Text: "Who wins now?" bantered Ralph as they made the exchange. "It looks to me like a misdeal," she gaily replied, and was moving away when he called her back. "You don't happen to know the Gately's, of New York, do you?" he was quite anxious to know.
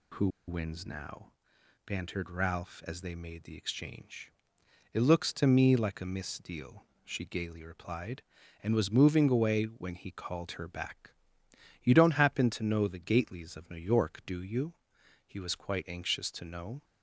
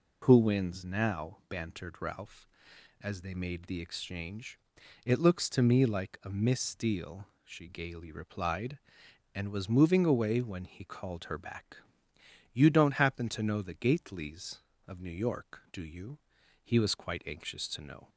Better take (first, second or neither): second